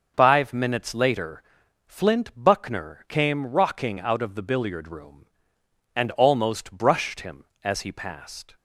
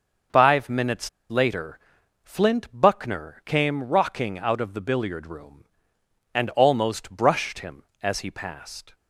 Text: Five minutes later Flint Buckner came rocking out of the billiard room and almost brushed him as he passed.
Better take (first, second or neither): first